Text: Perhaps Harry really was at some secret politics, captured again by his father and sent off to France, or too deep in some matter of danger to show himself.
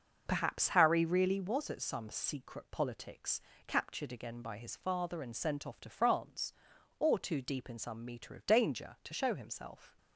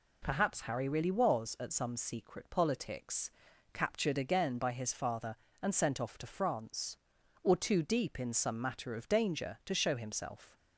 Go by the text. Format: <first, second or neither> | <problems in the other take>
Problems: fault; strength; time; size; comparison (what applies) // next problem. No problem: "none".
second | starts louder than the rest; until 1.2 s; 6.5 dB // says "meter" for "matter"; at 8.0 s